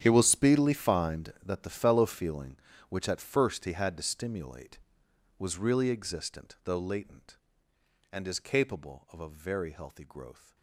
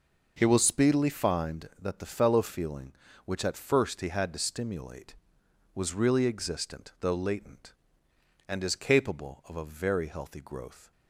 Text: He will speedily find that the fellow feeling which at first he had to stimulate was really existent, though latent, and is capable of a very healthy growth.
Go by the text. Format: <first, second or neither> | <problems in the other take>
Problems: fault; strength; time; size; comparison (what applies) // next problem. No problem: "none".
second | gets quieter; strong; throughout; 17.5 dB